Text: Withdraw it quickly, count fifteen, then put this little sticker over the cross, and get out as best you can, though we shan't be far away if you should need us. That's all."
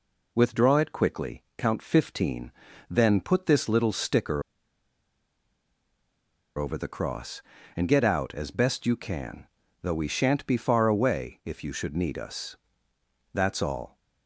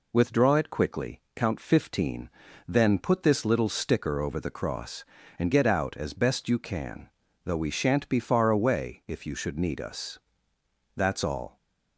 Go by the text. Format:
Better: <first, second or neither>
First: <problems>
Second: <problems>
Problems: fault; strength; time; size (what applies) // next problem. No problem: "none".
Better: second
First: pauses between "sticker" and "over"; strong; at 4.4 s; 2.1 s long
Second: none